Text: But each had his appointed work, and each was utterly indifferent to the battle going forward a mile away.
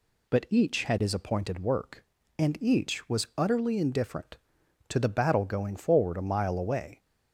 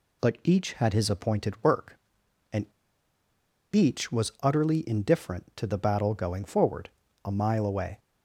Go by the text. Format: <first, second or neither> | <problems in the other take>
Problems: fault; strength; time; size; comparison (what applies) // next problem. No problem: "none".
first | pauses between "and" and "each"; at 2.6 s; 1.0 s long // pauses between "forward" and "a"; slight; at 6.8 s; 0.36 s long